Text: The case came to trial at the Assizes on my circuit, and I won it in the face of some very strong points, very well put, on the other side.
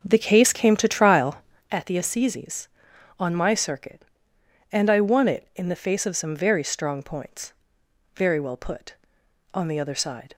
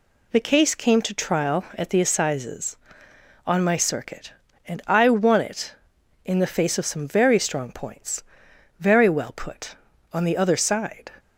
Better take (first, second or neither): second